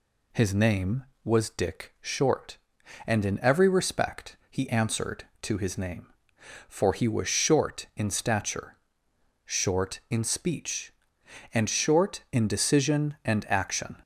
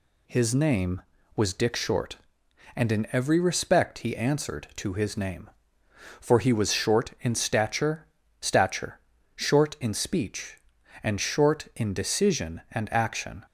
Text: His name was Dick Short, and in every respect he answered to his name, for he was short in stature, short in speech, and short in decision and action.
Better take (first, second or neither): first